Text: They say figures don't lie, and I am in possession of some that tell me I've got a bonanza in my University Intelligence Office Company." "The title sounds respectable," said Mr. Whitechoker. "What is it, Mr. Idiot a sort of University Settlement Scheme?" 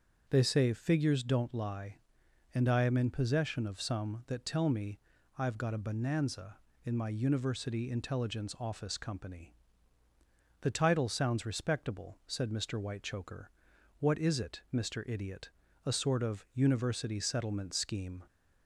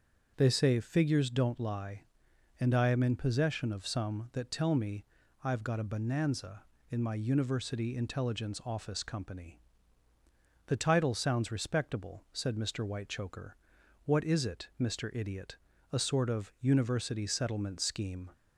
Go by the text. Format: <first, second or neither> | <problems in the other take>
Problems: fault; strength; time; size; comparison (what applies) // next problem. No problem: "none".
neither | starts louder than the rest; the same in both // pauses between "me" and "I've"; the same in both // pauses between "Idiot" and "a"; slight; the same in both